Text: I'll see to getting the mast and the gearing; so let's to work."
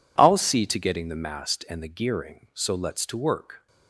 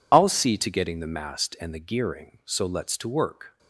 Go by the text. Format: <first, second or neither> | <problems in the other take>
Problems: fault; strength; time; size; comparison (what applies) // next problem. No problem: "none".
first | loses the start of "I'll"; at 0.1 s; 30 ms